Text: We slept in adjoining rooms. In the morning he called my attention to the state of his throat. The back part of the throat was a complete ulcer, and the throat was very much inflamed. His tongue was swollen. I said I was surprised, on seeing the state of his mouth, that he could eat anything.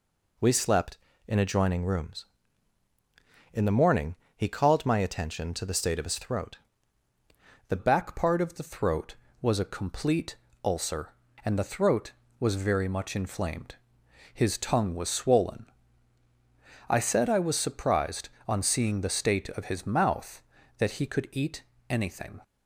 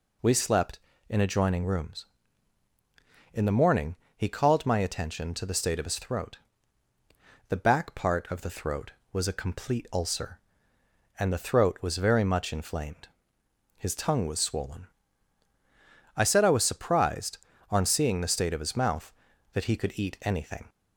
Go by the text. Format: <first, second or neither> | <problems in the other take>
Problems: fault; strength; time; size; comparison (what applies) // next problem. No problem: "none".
second | pauses between "morning" and "he"; slight; at 4.1 s; 0.20 s long; slight in the second // changes voice at "back"; from 7.7 s on; 14.6 s long // pauses between "complete" and "ulcer"; slight; at 10.3 s; 0.28 s long // pauses between "eat" and "anything"; slight; at 21.6 s; 0.26 s long